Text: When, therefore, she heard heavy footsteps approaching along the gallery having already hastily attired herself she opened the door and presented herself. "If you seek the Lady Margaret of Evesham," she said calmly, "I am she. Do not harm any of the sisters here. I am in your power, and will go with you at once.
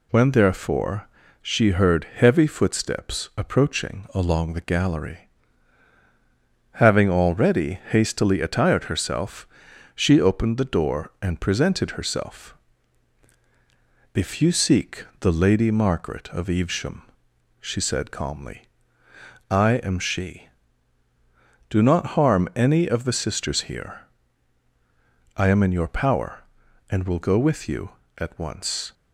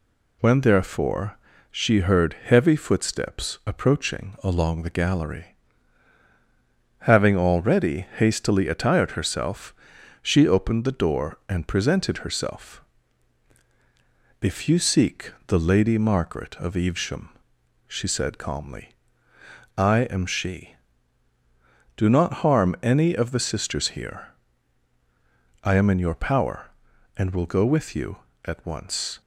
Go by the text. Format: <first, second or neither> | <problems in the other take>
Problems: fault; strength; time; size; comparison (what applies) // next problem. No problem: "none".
neither | pauses between "gallery" and "having"; strong; the same in both // pauses between "herself" and "she"; noticeable; the same in both